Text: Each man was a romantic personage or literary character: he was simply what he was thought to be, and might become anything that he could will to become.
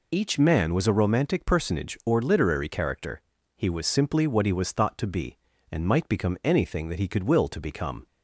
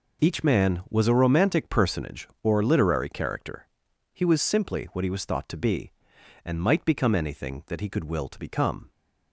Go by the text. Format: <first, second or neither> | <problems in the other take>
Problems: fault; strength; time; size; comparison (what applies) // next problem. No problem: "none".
neither | none